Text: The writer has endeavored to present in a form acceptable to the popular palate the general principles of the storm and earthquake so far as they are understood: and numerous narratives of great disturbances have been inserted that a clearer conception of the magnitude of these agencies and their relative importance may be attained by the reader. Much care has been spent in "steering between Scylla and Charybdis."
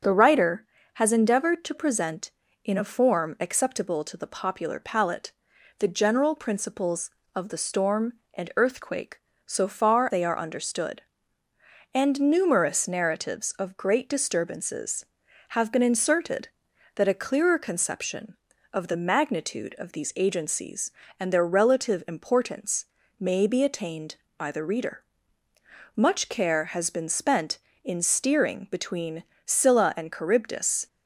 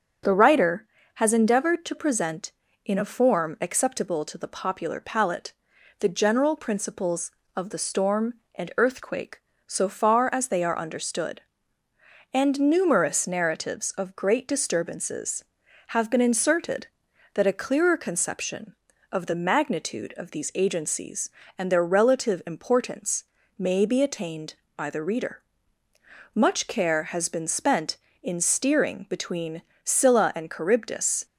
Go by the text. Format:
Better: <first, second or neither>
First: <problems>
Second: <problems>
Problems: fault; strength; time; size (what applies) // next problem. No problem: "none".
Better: second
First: starts louder than the rest; until 1.3 s; 6 dB // pauses between "palate" and "the"; noticeable; at 5.3 s; 0.46 s long // skips "as"; at 10.1 s // pauses between "importance" and "may"; slight; at 22.8 s; 0.32 s long // pauses between "between" and "Scylla"; slight; at 29.2 s; 0.24 s long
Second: starts louder than the rest; until 1.5 s; 6 dB // pauses between "palate" and "the"; noticeable; at 5.5 s; 0.46 s long // pauses between "importance" and "may"; slight; at 23.2 s; 0.32 s long // pauses between "between" and "Scylla"; slight; at 29.6 s; 0.24 s long